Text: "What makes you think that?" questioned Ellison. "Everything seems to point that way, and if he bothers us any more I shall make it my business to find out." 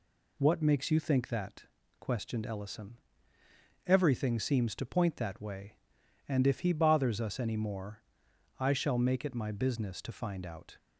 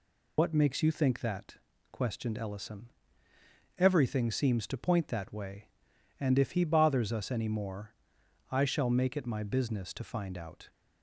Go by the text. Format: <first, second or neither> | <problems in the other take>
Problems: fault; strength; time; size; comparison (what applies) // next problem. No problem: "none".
first | loses the start of "What"; at 0.3 s; 75 ms // pauses between "more" and "I"; noticeable; at 7.9 s; 0.56 s long; noticeable in the first